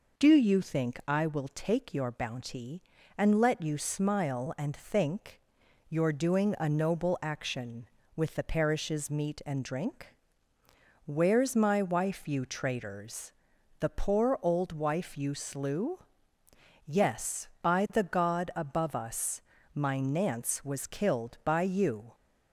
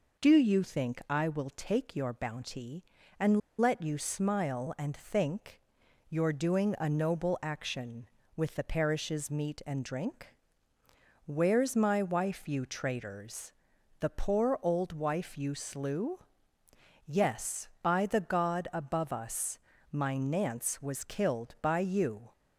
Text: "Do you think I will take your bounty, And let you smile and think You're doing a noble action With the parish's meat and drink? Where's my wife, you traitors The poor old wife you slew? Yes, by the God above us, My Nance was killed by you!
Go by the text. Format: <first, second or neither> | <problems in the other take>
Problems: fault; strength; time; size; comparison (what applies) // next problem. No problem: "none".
first | pauses between "And" and "let"; slight; at 3.3 s; 0.19 s long // pauses between "think" and "You're"; noticeable; at 5.6 s; 0.48 s long; noticeable in the first // pauses between "traitors" and "The"; noticeable; at 13.5 s; 0.48 s long; noticeable in the first